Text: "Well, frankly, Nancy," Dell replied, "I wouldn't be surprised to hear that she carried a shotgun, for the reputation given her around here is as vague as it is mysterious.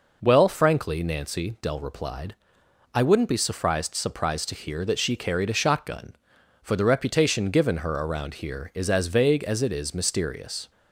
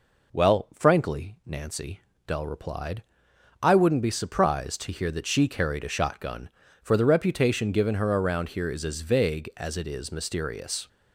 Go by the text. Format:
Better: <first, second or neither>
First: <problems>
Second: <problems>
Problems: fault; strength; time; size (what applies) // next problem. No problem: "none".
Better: second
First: says "surprised" twice; at 3.9 s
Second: none